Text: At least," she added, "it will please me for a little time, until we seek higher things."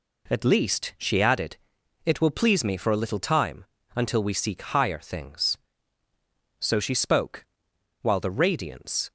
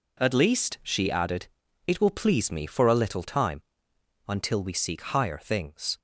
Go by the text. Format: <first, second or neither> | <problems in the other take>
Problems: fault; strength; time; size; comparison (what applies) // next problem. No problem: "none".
second | goes on to say "So she spoke while the radiance"; strong; from 6.5 s on; 2.5 s long